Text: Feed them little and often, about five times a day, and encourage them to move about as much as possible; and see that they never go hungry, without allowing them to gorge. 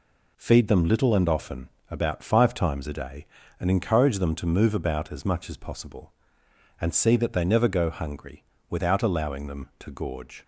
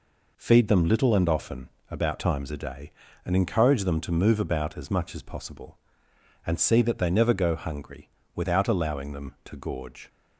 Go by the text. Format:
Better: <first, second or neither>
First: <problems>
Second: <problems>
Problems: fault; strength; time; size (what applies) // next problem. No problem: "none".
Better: first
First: none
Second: skips "five"; at 2.1 s